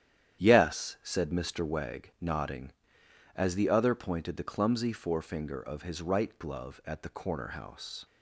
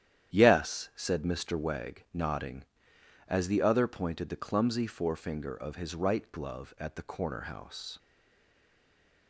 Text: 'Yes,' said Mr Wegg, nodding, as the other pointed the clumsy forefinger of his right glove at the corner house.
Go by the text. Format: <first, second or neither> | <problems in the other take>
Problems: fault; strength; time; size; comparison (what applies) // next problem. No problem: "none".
first | starts louder than the rest; strong; until 1.4 s; 10.5 dB; strong in the first // stays silent after the last word; noticeable; from 7.9 s on; 1.3 s long